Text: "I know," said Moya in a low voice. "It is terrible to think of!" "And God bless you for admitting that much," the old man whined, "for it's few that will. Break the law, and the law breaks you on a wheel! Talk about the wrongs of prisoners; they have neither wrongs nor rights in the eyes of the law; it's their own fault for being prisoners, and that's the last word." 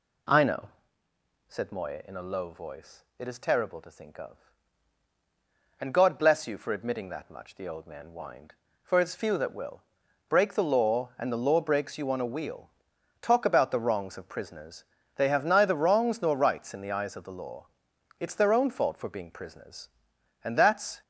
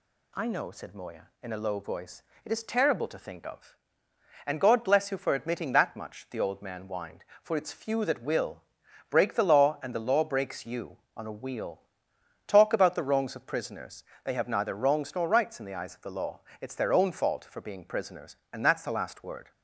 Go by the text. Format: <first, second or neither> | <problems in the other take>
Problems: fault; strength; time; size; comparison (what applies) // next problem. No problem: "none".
second | stops before "the last word"; at 21.0 s